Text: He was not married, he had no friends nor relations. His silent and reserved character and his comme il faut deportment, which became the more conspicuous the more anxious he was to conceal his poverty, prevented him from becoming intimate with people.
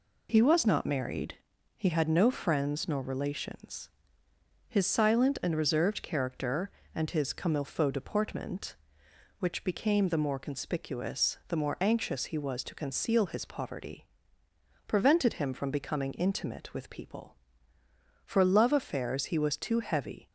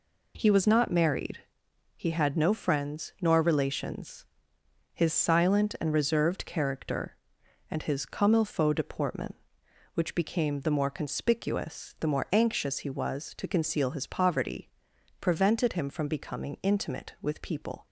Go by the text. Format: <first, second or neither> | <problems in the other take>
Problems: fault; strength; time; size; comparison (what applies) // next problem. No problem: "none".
second | goes on to say "For love affairs he was too heavy"; strong; from 18.2 s on; 2.0 s long